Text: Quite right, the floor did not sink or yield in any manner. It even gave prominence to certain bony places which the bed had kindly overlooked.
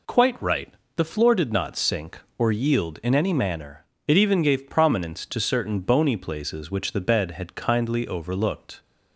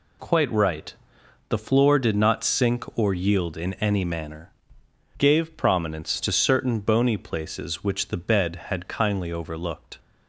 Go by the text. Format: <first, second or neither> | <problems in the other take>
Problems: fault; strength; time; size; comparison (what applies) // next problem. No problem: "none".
first | skips "It even"; at 4.8 s